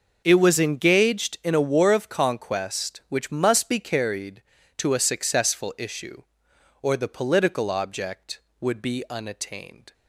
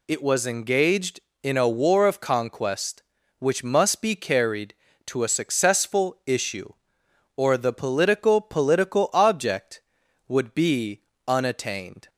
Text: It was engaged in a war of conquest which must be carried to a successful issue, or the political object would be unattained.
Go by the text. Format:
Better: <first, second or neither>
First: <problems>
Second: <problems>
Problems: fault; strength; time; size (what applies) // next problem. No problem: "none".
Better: first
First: none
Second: says "political" twice; at 8.4 s // pauses between "be" and "unattained"; slight; at 11.0 s; 0.26 s long